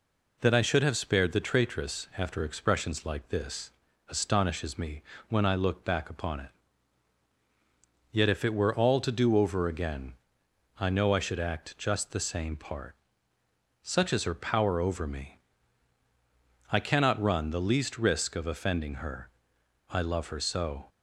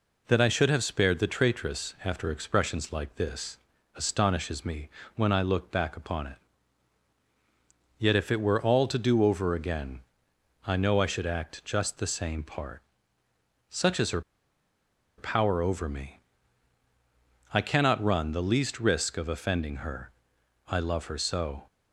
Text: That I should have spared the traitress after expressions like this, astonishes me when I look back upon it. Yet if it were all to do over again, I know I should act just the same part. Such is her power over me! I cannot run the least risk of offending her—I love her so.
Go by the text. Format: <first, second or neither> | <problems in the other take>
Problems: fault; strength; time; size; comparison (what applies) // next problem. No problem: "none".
first | pauses between "me" and "when"; slight; at 4.8 s; 0.28 s long; slight in the first // pauses between "her" and "power"; noticeable; at 14.2 s; 0.97 s long